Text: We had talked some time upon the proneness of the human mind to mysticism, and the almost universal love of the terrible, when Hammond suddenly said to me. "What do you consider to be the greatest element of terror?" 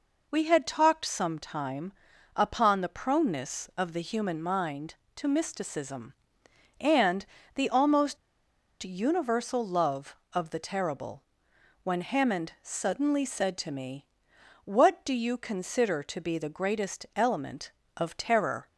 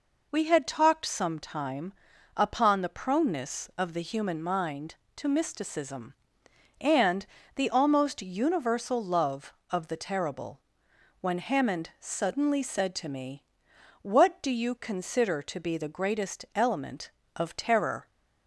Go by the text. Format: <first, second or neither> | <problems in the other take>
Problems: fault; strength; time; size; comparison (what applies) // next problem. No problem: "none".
second | pauses between "time" and "upon"; at 1.9 s; 0.42 s long; also in the second // pauses between "and" and "the"; slight; at 7.2 s; 0.30 s long; slight in the second // pauses between "almost" and "universal"; noticeable; at 8.1 s; 0.65 s long